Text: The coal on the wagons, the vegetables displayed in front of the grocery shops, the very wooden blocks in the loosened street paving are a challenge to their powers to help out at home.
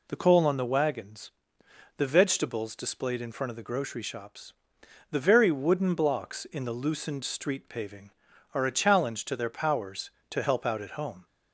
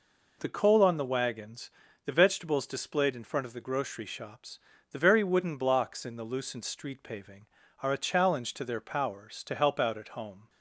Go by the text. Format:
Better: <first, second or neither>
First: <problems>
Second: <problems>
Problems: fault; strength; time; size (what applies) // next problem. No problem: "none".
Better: neither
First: none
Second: none